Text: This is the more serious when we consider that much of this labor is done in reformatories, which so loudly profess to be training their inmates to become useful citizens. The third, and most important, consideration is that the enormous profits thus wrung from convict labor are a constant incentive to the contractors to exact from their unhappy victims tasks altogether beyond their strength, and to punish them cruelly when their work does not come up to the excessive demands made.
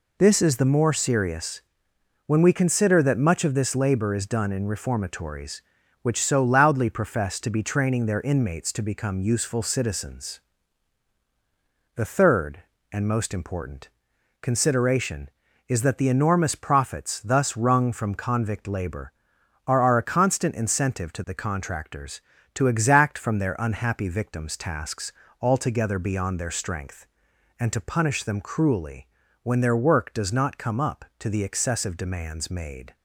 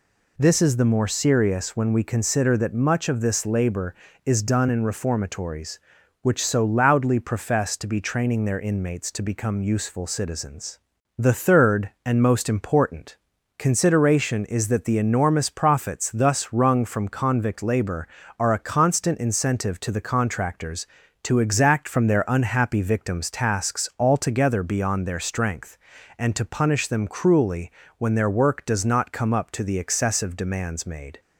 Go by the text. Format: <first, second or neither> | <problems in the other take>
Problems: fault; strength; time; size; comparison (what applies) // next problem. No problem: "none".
second | pauses between "serious" and "when"; noticeable; at 1.6 s; 0.66 s long // says "are" twice; at 19.8 s // pauses between "tasks" and "altogether"; slight; at 25.1 s; 0.30 s long // pauses between "cruelly" and "when"; slight; at 29.0 s; 0.34 s long; slight in the second